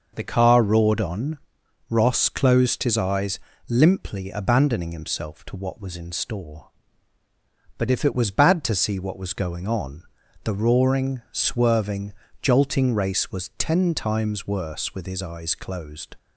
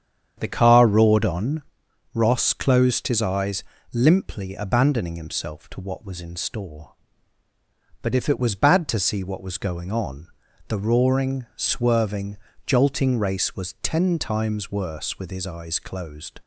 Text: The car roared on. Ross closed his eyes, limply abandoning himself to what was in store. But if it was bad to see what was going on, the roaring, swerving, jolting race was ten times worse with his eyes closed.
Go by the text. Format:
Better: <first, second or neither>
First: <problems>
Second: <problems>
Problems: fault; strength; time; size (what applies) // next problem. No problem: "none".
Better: first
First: none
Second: starts louder than the rest; strong; until 1.8 s; 8.5 dB